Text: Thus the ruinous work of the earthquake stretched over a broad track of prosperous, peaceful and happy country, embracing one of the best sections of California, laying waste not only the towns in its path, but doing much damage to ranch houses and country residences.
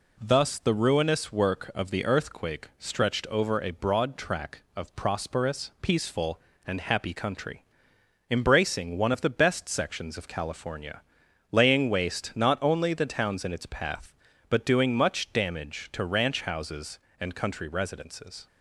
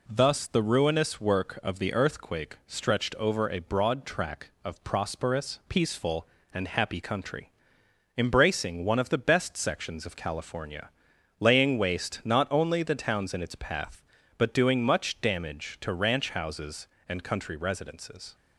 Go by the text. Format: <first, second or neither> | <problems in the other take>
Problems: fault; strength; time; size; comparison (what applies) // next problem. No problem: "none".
neither | none